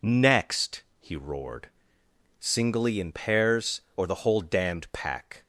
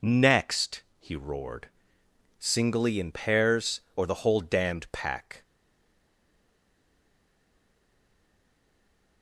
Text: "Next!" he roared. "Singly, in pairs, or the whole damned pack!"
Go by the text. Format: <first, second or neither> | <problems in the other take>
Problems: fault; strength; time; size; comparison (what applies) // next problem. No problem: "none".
first | stays silent after the last word; strong; from 5.4 s on; 3.8 s long